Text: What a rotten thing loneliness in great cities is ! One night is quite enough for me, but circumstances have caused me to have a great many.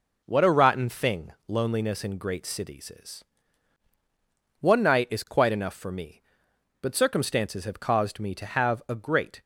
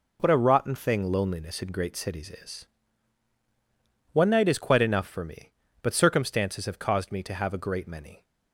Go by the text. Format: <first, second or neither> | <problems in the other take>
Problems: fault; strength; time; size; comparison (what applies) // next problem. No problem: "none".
second | pauses between "thing" and "loneliness"; slight; at 1.3 s; 0.16 s long // stops before "many"; at 9.4 s